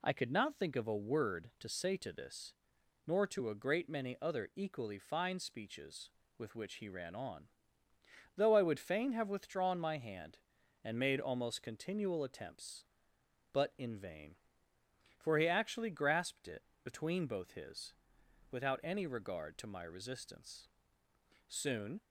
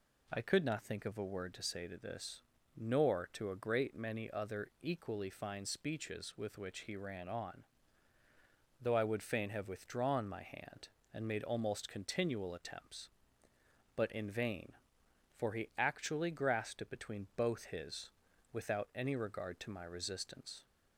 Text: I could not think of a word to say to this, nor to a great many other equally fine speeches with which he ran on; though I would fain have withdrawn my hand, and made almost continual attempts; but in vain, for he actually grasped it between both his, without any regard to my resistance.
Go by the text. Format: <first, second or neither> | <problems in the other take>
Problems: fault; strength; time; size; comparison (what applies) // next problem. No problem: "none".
second | pauses between "it" and "between"; slight; at 16.6 s; 0.20 s long // goes on to say "Soon"; from 21.4 s on; 0.54 s long